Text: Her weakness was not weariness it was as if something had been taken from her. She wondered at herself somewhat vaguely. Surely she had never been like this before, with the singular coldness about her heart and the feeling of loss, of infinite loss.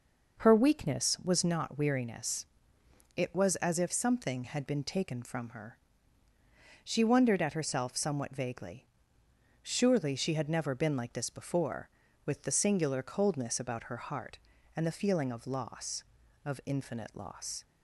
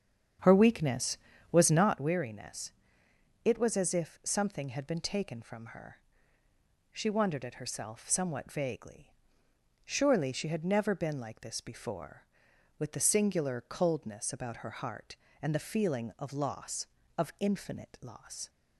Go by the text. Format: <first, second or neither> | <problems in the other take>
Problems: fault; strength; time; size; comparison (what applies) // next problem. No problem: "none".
first | starts louder than the rest; strong; until 2.0 s; 8 dB // pauses between "weariness" and "it"; noticeable; at 2.7 s; 0.74 s long; noticeable in the first